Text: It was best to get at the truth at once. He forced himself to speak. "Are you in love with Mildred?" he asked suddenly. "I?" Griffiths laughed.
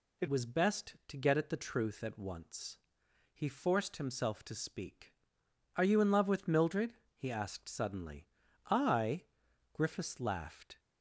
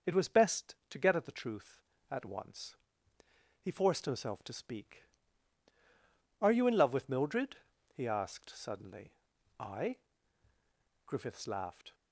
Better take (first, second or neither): second